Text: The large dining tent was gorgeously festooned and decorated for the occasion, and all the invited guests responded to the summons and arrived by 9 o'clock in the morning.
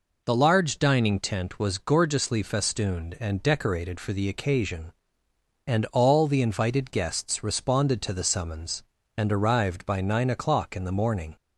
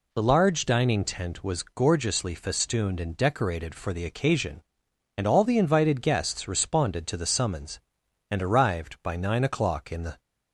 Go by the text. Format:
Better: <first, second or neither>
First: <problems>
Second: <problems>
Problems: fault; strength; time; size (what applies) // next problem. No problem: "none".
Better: first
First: none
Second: stops before "morning"; at 10.1 s